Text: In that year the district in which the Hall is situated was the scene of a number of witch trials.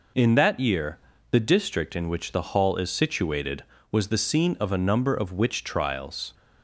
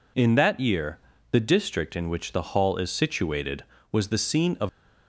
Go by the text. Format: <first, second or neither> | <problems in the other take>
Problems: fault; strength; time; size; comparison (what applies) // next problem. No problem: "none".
first | pauses between "year" and "the"; slight; at 0.9 s; 0.32 s long; slight in the first // stops before "a number of witch trials"; at 4.6 s